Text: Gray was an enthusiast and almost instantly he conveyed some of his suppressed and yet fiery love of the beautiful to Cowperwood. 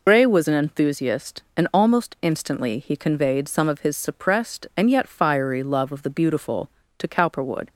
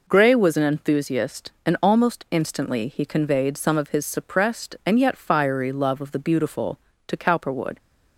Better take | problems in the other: second | loses the start of "Gray"; at 0.0 s; 70 ms

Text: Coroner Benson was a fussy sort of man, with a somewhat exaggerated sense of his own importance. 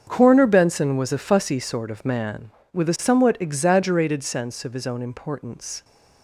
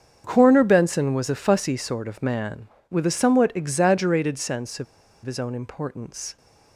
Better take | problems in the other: first | starts louder than the rest; strong; until 1.2 s; 7.5 dB; strong in the first // pauses between "of" and "his"; at 4.8 s; 0.39 s long

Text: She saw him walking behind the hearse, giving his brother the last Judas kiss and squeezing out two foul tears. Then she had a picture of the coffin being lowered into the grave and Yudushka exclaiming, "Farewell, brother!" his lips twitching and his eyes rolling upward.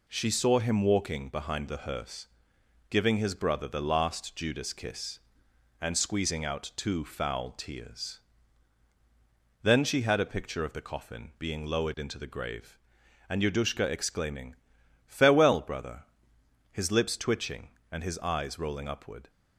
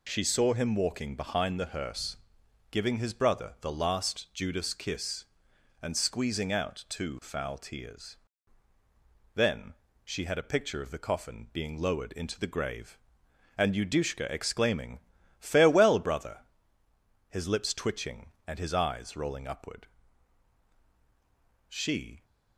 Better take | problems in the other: first | pauses between "Then" and "she"; slight; at 9.7 s; 0.30 s long // goes on to say "She"; from 21.6 s on; 0.56 s long

